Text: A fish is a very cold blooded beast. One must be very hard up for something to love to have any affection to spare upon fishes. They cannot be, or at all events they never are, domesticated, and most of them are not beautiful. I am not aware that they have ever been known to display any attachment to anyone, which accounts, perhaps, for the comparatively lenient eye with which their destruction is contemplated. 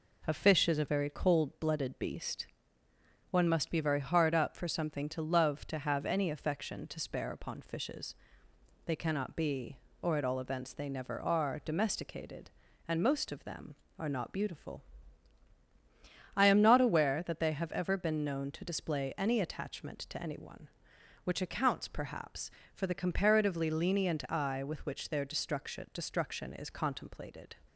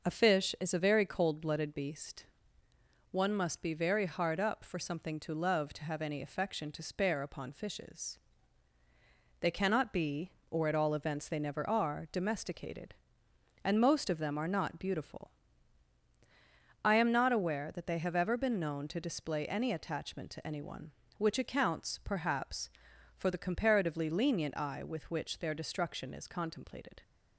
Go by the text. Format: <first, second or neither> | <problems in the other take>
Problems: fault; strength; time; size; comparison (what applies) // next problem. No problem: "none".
second | says "destruction" twice; at 25.9 s